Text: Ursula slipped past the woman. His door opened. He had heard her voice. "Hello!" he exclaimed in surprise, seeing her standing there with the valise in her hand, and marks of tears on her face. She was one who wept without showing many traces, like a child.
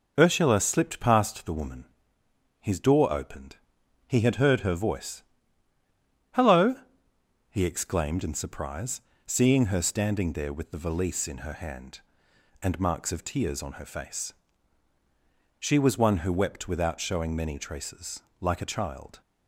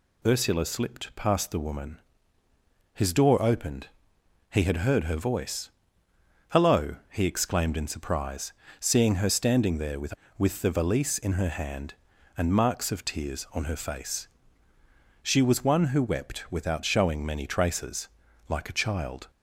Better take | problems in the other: first | says "with" twice; at 10.3 s

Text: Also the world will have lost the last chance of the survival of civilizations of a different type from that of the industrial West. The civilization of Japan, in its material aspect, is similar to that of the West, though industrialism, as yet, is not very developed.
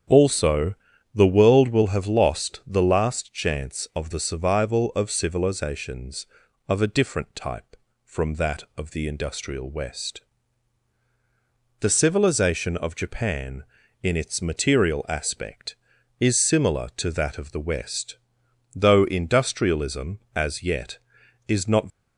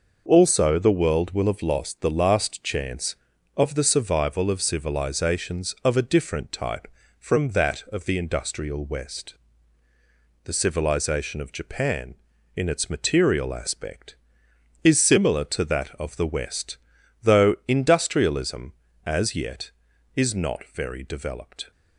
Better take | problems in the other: second | starts louder than the rest; strong; until 1.4 s; 8.5 dB // pauses between "Also" and "the"; at 0.7 s; 0.40 s long // stops before "very developed"; at 21.8 s

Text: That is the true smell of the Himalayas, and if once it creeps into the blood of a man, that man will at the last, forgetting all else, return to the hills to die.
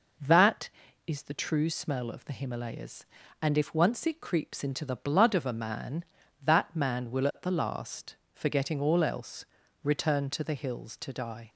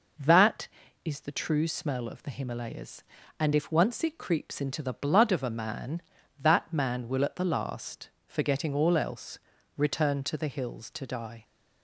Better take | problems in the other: neither | none

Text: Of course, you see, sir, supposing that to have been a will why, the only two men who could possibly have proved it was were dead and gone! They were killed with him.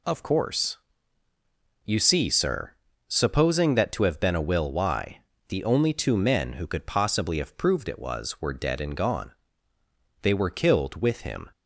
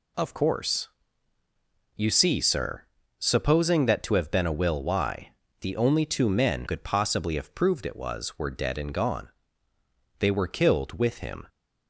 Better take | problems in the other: first | skips "who"; at 6.6 s

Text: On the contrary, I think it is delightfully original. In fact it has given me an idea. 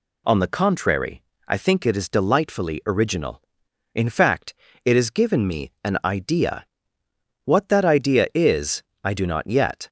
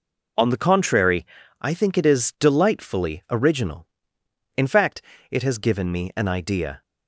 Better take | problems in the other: second | pauses between "fact" and "it"; slight; at 4.5 s; 0.30 s long; slight in the second // goes on to say "What that idea is I do not yet"; strong; from 7.4 s on; 2.4 s long

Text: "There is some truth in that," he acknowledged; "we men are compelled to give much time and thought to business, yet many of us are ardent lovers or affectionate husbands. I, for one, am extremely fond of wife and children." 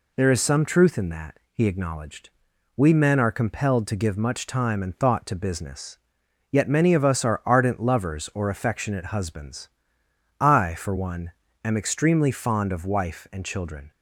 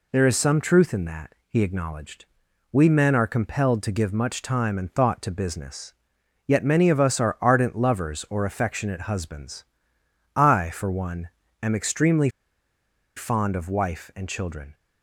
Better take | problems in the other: first | pauses between "extremely" and "fond"; noticeable; at 12.2 s; 0.87 s long

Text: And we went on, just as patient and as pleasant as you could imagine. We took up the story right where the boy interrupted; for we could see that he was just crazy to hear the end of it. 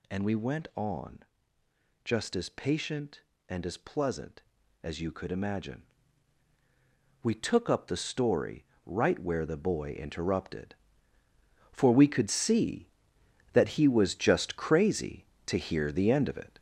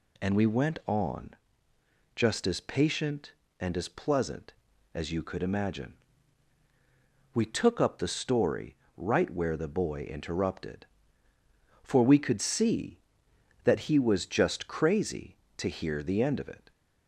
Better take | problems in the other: second | gets louder; noticeable; throughout; 5.5 dB // pauses between "story" and "right"; slight; at 8.6 s; 0.22 s long; slight in the second

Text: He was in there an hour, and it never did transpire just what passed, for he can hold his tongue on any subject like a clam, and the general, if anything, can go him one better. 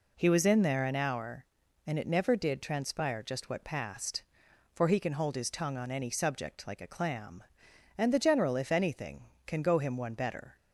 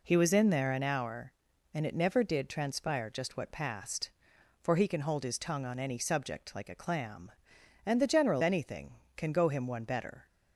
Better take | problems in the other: first | skips "if"; at 8.4 s

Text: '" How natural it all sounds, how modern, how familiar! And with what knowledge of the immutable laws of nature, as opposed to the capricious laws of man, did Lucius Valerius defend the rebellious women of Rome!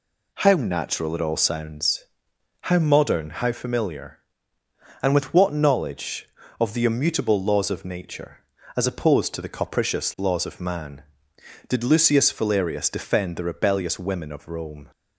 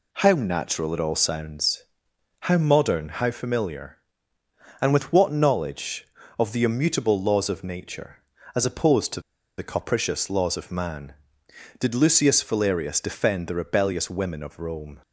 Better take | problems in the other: first | pauses between "to" and "the"; at 9.2 s; 0.36 s long

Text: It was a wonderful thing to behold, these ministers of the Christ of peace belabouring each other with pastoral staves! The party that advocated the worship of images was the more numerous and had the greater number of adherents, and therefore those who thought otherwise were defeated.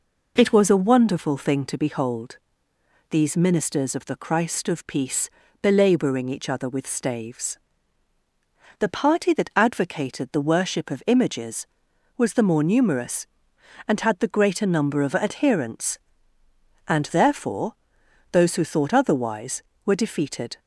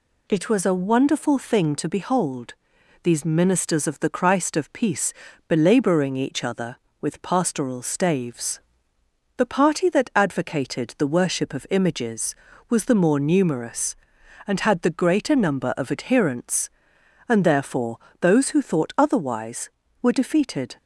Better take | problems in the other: second | pauses between "peace" and "belabouring"; slight; at 5.3 s; 0.32 s long; slight in the second // skips "pastoral"; at 6.8 s // pauses between "therefore" and "those"; noticeable; at 17.7 s; 0.60 s long; slight in the second

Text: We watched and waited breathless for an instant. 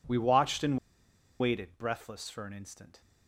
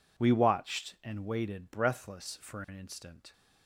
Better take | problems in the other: second | pauses between "and" and "waited"; noticeable; at 0.7 s; 0.63 s long

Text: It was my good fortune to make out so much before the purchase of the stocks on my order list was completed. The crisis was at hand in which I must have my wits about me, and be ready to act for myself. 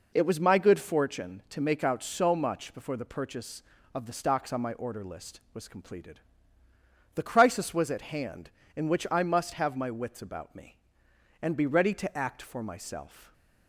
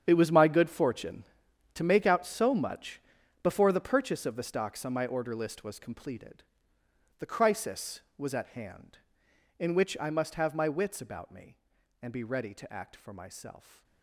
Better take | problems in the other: first | gets quieter; strong; throughout; 14.5 dB // pauses between "much" and "before"; at 2.9 s; 0.44 s long

